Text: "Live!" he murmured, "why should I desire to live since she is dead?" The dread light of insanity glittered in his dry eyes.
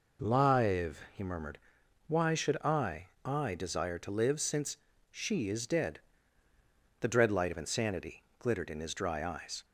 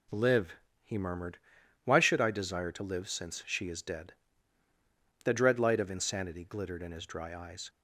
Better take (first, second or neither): second